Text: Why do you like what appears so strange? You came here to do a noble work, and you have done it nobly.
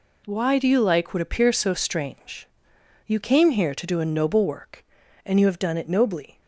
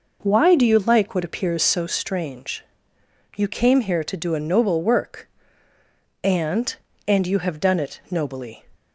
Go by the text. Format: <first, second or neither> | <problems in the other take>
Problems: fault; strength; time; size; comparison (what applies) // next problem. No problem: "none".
first | says "and" twice; at 7.0 s